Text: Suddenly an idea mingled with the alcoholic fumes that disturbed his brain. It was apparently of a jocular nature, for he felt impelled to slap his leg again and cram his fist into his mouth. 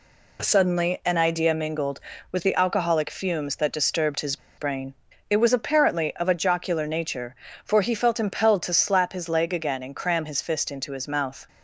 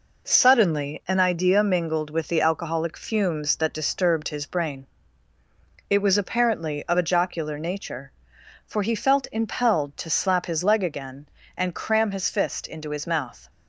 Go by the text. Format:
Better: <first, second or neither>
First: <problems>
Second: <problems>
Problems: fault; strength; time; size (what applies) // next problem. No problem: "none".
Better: second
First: pauses between "his" and "brain"; slight; at 4.3 s; 0.20 s long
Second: none